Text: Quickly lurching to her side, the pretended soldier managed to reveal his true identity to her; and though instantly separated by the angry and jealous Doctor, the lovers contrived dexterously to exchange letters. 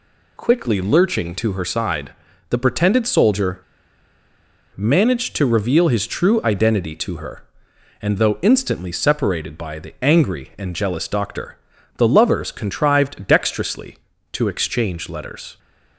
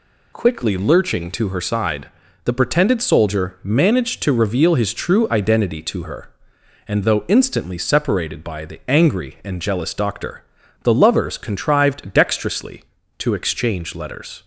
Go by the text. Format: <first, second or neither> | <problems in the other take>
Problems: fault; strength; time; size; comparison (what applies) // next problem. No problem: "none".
second | pauses between "soldier" and "managed"; at 3.6 s; 1.1 s long